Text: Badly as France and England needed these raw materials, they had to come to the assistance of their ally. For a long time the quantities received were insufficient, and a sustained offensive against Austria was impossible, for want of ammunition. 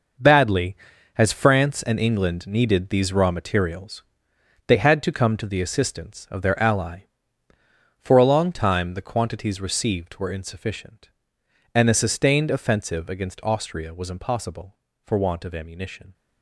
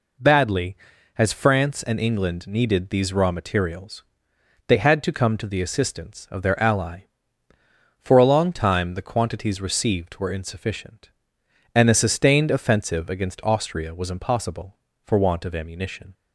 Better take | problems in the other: second | gets quieter; strong; throughout; 10.5 dB

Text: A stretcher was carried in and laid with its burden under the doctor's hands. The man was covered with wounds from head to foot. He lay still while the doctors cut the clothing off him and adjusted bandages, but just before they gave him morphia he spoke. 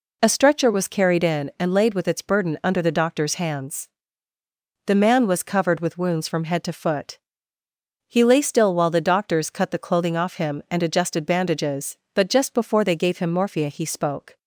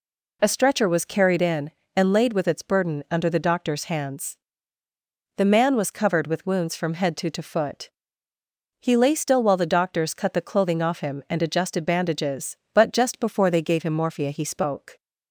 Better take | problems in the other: first | says "to" twice; at 7.2 s

